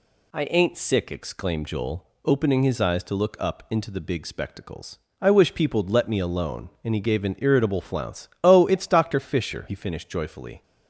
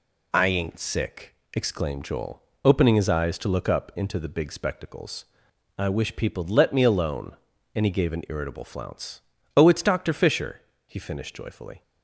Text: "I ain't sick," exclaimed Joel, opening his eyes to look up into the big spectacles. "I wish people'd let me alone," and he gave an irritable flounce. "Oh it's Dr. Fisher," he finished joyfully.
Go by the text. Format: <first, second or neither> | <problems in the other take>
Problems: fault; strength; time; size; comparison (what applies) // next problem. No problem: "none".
neither | none